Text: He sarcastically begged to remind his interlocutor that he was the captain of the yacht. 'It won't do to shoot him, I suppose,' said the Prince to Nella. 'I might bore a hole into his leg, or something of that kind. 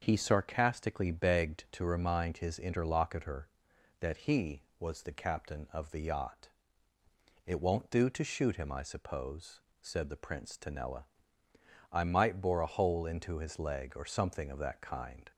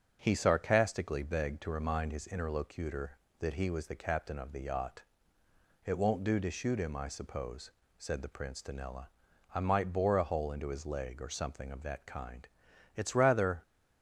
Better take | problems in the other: first | starts louder than the rest; until 1.2 s; 7 dB; also in the first // goes on to say "It's rather"; noticeable; from 12.9 s on; 0.66 s long

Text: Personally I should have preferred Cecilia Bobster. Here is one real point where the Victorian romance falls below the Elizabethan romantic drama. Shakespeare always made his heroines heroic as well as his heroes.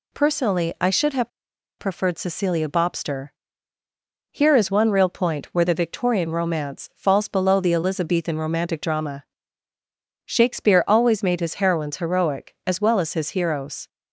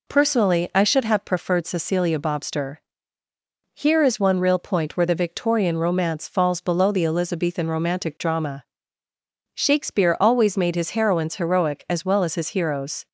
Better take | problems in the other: second | pauses between "have" and "preferred"; noticeable; at 1.2 s; 0.49 s long

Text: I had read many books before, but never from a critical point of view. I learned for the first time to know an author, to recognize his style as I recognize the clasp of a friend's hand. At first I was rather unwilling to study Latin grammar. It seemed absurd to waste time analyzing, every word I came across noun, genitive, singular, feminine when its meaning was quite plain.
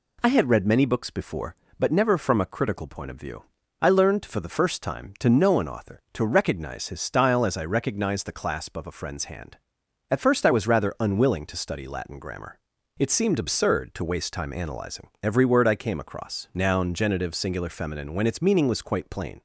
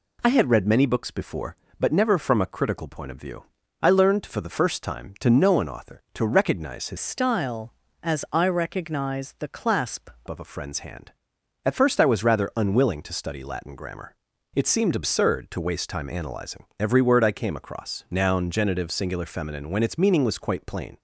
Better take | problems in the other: first | changes voice from "style" to "clasp"; from 6.9 to 10.0 s; 3.1 s long

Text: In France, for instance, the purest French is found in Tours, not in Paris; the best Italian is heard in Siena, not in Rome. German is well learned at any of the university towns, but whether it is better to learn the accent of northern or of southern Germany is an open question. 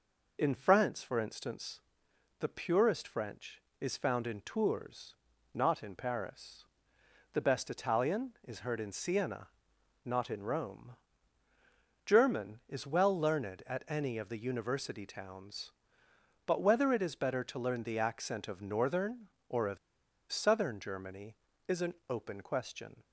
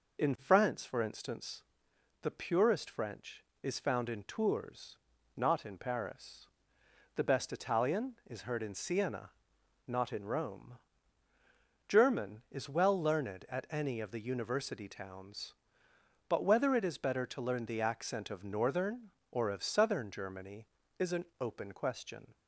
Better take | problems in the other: second | pauses between "of" and "southern"; noticeable; at 19.7 s; 0.54 s long // pauses between "an" and "open"; slight; at 21.9 s; 0.16 s long; slight in the second

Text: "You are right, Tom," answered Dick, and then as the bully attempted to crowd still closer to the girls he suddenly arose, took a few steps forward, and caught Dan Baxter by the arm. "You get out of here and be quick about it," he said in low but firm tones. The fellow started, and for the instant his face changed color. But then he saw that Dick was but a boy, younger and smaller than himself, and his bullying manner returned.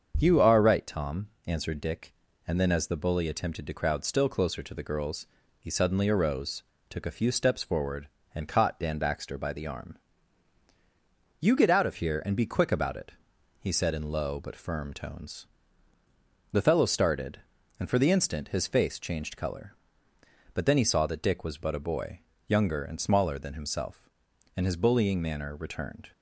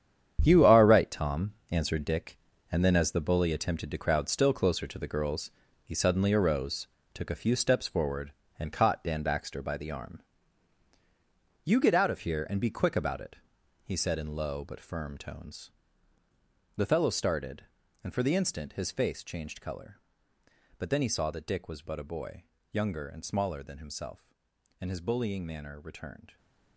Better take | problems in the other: first | gets quieter; strong; throughout; 11 dB // starts louder than the rest; strong; until 1.4 s; 8.5 dB; also in the first // pauses between "girls" and "he"; slight; at 5.5 s; 0.34 s long; slight in the first

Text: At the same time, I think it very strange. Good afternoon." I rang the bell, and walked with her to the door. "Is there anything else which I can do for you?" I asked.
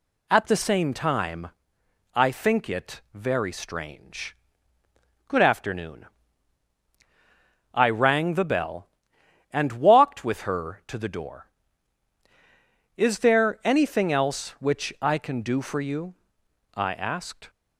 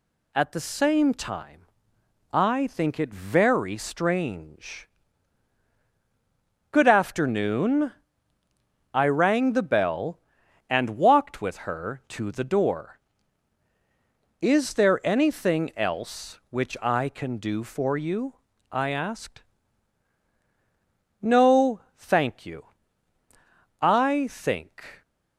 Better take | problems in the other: first | goes on to say "No thank you I think"; strong; from 21.2 s on; 3.8 s long

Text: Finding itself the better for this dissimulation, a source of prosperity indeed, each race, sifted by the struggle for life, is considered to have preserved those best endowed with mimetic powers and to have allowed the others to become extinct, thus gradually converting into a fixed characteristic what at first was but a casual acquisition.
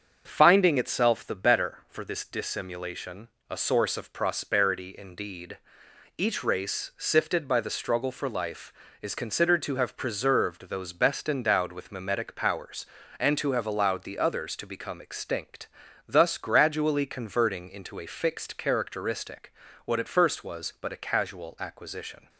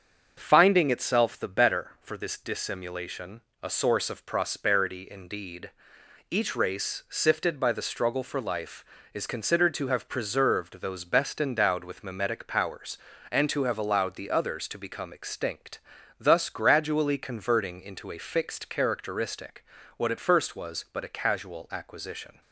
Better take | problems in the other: neither | starts louder than the rest; the same in both // pauses between "characteristic" and "what"; slight; the same in both

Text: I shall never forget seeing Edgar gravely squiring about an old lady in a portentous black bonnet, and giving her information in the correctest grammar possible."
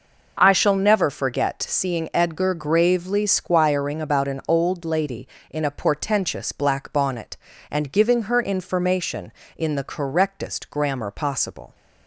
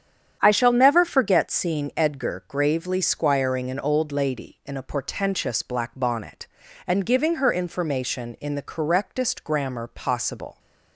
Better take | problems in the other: first | starts louder than the rest; strong; until 1.4 s; 8.5 dB // skips "about"; at 3.7 s

